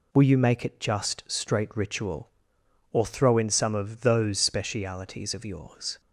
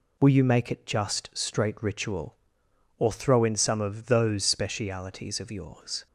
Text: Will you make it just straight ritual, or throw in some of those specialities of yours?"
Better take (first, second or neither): neither